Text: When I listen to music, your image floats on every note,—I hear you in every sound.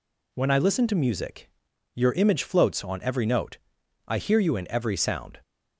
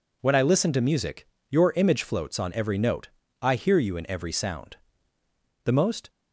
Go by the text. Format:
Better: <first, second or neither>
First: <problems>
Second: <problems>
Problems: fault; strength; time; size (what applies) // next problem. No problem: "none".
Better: first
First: none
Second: goes on to say "The most"; slight; from 5.6 s on; 0.46 s long